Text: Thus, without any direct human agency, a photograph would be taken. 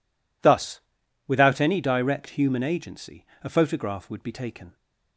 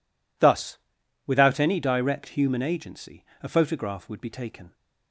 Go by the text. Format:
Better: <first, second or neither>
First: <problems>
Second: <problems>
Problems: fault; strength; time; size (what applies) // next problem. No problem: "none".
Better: neither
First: none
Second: none